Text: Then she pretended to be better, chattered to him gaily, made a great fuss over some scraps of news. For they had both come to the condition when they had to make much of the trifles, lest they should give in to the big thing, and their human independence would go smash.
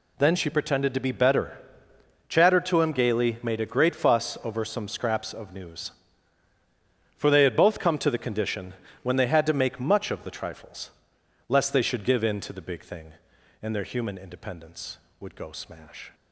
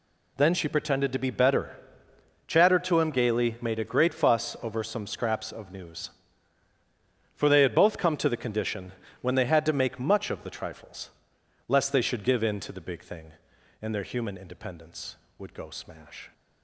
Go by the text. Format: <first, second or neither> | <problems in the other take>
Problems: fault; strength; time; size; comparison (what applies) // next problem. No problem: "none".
neither | pauses between "condition" and "when"; slight; the same in both